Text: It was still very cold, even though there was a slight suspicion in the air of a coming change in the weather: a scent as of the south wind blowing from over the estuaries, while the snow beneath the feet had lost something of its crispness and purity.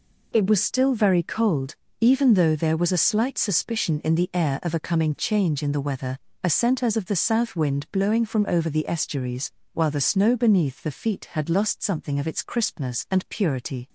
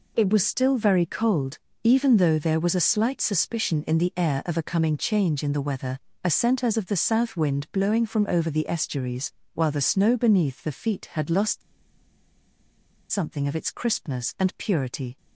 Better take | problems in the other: first | pauses between "lost" and "something"; strong; at 11.6 s; 1.5 s long

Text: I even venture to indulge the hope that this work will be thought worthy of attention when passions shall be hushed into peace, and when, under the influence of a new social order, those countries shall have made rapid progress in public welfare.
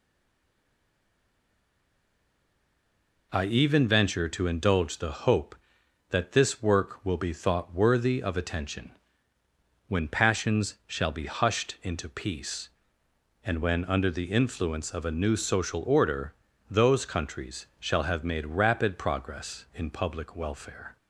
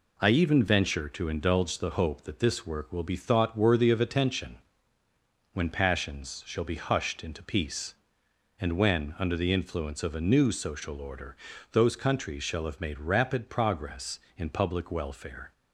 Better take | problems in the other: second | stays silent before the first word; strong; until 3.3 s; 3.3 s long // pauses between "attention" and "when"; noticeable; at 8.9 s; 0.96 s long; noticeable in the second

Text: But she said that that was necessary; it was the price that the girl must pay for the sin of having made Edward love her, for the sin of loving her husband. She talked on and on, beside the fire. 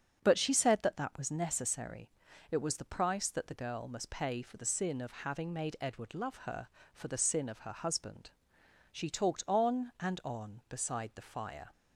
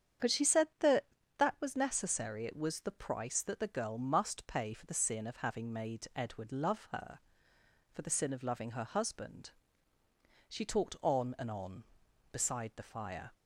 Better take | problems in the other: second | starts louder than the rest; strong; until 1.2 s; 7 dB; strong in the second // skips "loving"; at 7.5 s

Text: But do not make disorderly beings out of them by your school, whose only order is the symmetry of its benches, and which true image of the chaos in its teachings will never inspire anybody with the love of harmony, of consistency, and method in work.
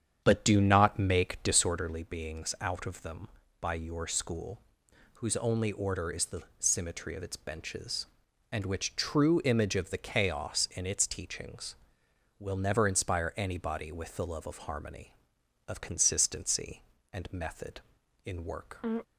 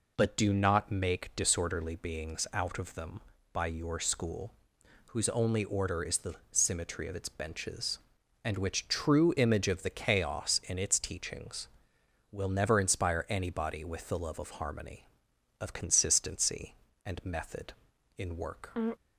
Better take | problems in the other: second | starts louder than the rest; strong; until 1.8 s; 8.5 dB // pauses between "the" and "symmetry"; slight; at 6.4 s; 0.16 s long; slight in the second

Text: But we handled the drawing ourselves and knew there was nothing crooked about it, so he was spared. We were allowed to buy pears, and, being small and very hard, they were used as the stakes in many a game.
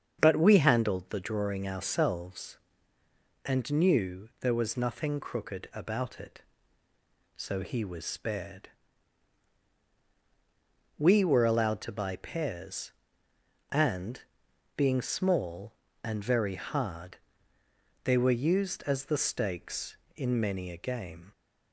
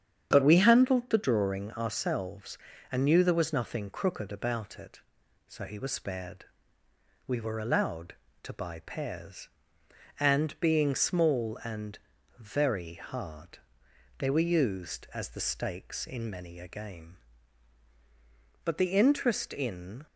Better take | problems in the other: first | starts louder than the rest; strong; until 1.3 s; 8.5 dB; strong in the first // pauses between "and" and "very"; at 11.9 s; 0.40 s long // goes on to say "But the interest in"; from 18.6 s on; 1.4 s long

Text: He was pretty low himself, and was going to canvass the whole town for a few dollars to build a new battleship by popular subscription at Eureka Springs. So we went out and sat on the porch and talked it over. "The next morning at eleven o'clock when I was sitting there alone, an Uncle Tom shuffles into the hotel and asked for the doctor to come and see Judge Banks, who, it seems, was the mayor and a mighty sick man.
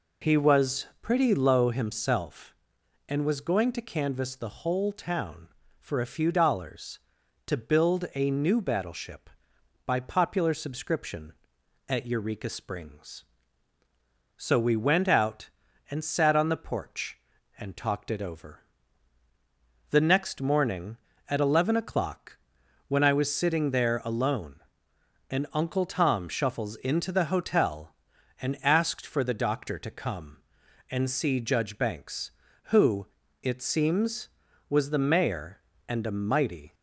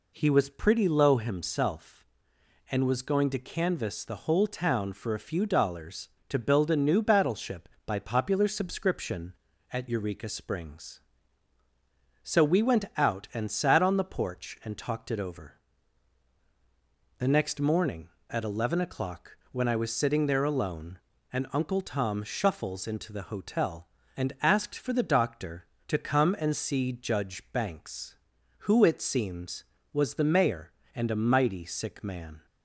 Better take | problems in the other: second | pauses between "o'clock" and "when"; noticeable; at 22.3 s; 0.50 s long; slight in the second // stops before "sick man"; at 36.7 s

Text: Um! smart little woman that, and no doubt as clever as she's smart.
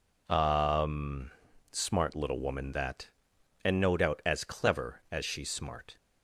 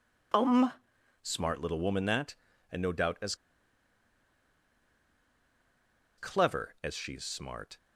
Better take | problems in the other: first | pauses between "as" and "clever"; strong; at 3.3 s; 2.8 s long

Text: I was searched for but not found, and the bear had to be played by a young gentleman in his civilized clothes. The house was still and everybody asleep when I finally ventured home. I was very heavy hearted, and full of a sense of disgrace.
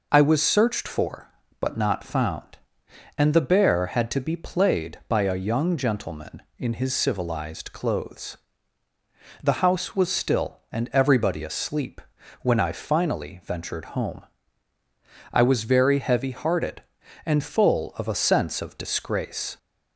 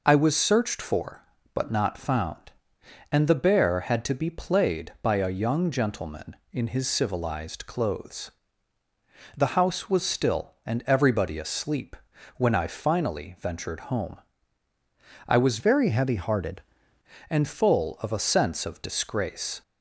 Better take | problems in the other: first | pauses between "asleep" and "when"; at 11.9 s; 0.42 s long; also in the first // changes voice from "very" to "hearted"; from 15.5 to 16.6 s; 1.1 s long

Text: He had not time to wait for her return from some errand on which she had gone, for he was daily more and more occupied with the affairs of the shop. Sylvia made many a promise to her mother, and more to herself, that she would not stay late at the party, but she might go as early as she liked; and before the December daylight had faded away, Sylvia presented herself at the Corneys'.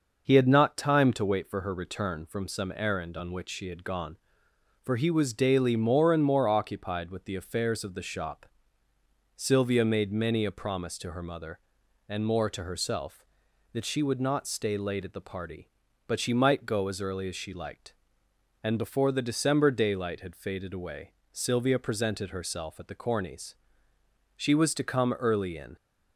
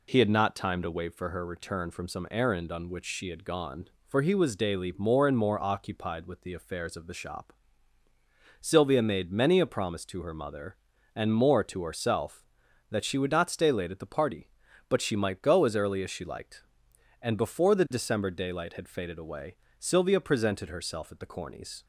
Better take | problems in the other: second | starts louder than the rest; noticeable; until 1.2 s; 6 dB // goes on to say "She was to come early in"; from 24.3 s on; 1.3 s long

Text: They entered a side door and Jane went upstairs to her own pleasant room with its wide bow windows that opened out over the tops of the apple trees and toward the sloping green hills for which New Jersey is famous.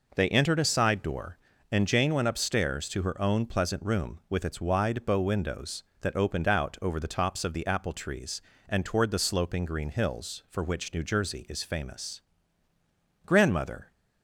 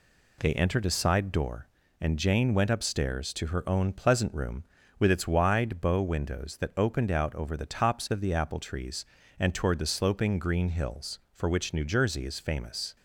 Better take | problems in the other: second | goes on to say "Grandmother"; noticeable; from 13.2 s on; 0.64 s long

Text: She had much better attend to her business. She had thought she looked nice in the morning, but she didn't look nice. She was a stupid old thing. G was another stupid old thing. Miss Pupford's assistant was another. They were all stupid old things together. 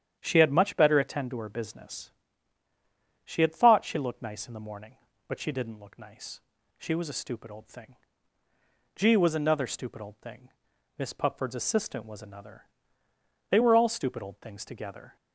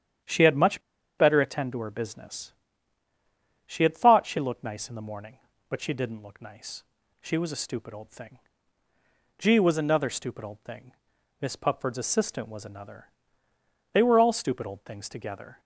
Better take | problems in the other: first | starts louder than the rest; strong; until 1.6 s; 9.5 dB; strong in the first // pauses between "much" and "better"; at 0.8 s; 0.37 s long

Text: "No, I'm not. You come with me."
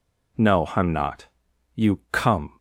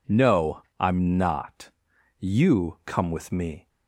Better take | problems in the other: second | stops before "with me"; at 2.5 s

